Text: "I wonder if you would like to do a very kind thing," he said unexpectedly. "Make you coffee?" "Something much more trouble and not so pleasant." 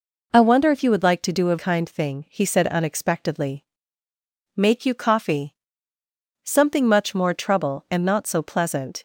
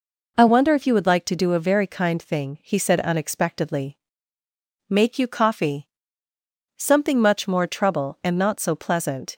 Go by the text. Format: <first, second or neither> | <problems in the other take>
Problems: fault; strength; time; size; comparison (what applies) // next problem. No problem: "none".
second | skips "very"; at 1.5 s